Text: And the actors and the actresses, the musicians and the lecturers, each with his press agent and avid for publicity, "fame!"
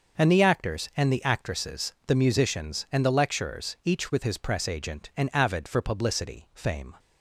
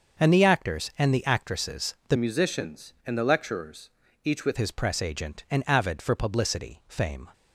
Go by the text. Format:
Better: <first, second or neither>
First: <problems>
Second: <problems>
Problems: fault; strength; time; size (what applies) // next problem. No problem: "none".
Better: first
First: starts louder than the rest; until 1.2 s; 6 dB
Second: starts louder than the rest; until 1.3 s; 6.5 dB // changes voice from "musicians" to "with"; from 2.1 to 4.5 s; 2.4 s long